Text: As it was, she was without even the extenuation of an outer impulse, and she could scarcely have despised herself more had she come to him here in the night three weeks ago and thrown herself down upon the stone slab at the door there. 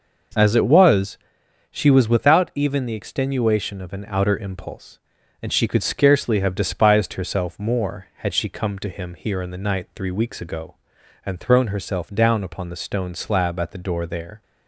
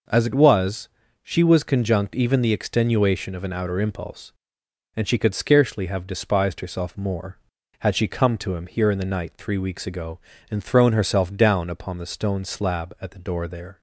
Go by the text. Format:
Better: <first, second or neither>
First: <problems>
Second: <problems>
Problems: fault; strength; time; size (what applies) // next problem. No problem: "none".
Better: first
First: none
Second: says "conjunct" for "without"; at 1.6 s